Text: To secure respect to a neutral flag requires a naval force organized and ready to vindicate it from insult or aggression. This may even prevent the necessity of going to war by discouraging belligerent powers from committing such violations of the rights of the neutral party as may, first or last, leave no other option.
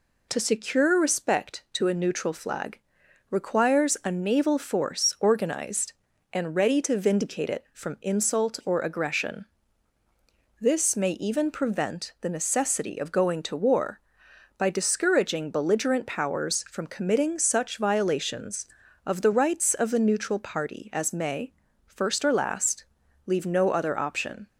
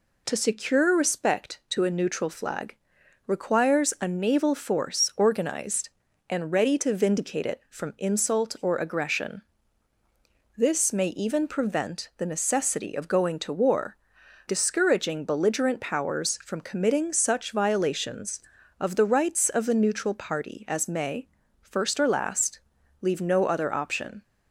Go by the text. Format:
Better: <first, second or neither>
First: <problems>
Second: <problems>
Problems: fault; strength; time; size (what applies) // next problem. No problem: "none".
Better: first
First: pauses between "flag" and "requires"; noticeable; at 2.8 s; 0.50 s long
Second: pauses between "flag" and "requires"; noticeable; at 2.7 s; 0.50 s long // skips "by"; at 14.2 s